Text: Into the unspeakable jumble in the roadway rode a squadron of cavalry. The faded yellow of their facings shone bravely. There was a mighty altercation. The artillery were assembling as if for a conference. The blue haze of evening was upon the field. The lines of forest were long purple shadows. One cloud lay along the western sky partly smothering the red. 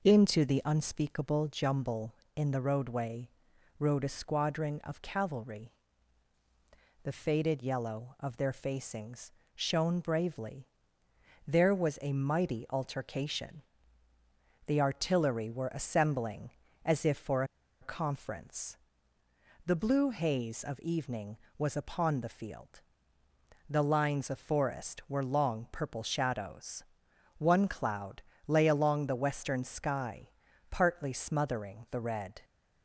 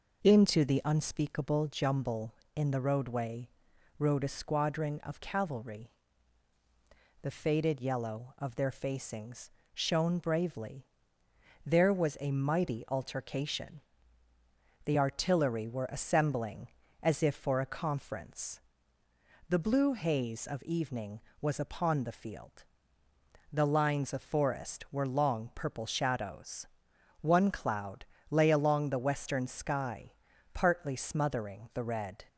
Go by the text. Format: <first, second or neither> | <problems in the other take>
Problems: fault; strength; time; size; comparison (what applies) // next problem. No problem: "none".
second | pauses between "roadway" and "rode"; noticeable; at 3.2 s; 0.48 s long; noticeable in the second // pauses between "facings" and "shone"; slight; at 9.2 s; 0.24 s long; slight in the second // pauses between "for" and "a"; at 17.4 s; 0.37 s long // pauses between "cloud" and "lay"; slight; at 28.2 s; 0.28 s long; slight in the second // pauses between "sky" and "partly"; at 30.2 s; 0.40 s long; also in the second